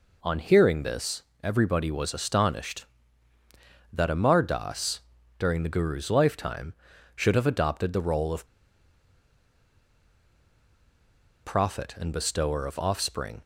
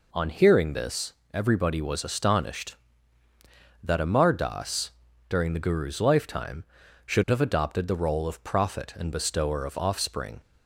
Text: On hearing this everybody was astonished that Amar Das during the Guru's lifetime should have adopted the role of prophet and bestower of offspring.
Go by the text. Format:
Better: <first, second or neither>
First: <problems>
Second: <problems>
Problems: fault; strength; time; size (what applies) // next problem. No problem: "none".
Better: second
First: pauses between "this" and "everybody"; slight; at 1.2 s; 0.20 s long // pauses between "Das" and "during"; at 5.0 s; 0.38 s long // pauses between "of" and "prophet"; strong; at 8.4 s; 2.9 s long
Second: pauses between "this" and "everybody"; slight; at 1.1 s; 0.20 s long // pauses between "Das" and "during"; at 4.9 s; 0.38 s long